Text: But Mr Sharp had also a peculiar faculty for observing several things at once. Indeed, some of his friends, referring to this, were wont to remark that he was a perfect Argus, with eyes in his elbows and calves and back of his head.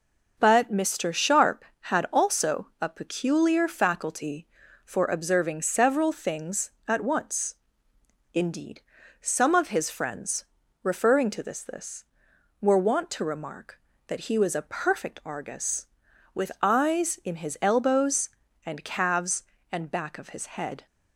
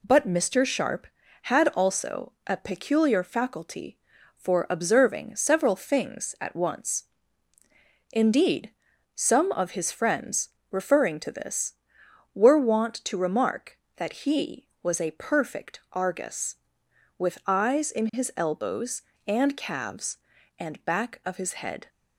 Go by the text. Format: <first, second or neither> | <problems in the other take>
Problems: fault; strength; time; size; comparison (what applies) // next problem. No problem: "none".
second | says "this" twice; at 11.6 s